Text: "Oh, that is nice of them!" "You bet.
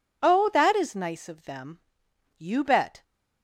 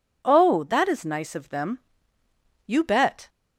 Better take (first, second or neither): neither